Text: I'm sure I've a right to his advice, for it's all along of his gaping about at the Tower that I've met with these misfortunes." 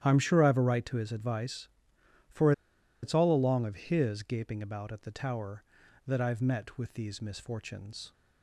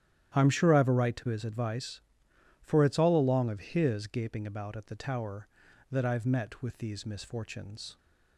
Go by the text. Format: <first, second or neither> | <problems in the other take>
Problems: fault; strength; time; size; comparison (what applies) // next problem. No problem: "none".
second | starts louder than the rest; strong; until 1.0 s; 11 dB; strong in the second // pauses between "for" and "it's"; noticeable; at 2.5 s; 0.50 s long